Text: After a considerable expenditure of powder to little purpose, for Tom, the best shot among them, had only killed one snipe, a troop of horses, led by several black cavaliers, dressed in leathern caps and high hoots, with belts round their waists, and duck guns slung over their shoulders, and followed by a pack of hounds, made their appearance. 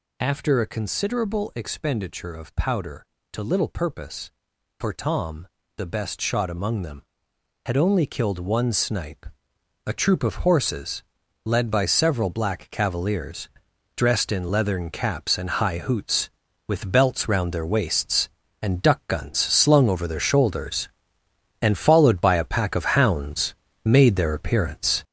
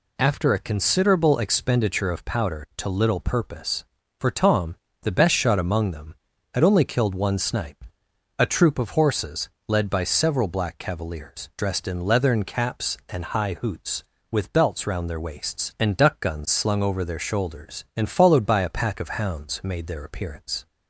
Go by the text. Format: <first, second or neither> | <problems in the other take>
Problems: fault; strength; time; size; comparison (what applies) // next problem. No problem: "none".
second | gets louder; strong; throughout; 7 dB